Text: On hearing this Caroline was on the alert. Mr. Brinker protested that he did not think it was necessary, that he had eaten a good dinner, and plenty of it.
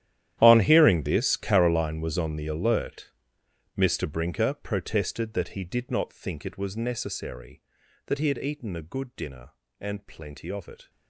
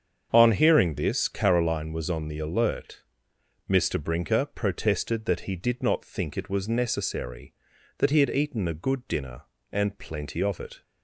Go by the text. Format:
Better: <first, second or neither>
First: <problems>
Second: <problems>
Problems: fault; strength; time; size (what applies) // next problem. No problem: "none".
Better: second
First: gets quieter; strong; throughout; 19 dB // starts louder than the rest; strong; until 1.4 s; 11.5 dB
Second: starts louder than the rest; strong; until 1.3 s; 7.5 dB